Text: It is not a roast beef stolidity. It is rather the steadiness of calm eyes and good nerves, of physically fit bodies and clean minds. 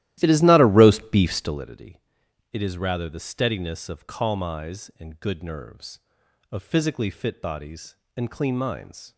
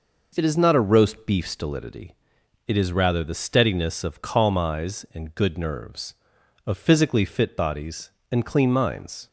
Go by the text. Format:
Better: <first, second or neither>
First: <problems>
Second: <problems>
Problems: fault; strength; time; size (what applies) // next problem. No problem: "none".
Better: second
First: starts louder than the rest; strong; until 1.6 s; 14.5 dB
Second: none